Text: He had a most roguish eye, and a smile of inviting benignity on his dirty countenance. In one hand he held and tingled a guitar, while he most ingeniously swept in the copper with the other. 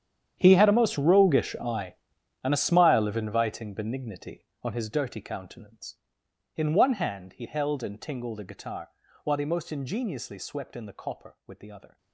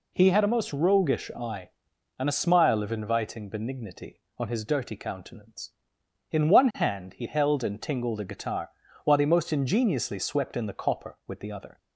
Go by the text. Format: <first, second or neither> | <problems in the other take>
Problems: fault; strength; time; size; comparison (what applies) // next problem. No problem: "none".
second | gets quieter; strong; throughout; 17 dB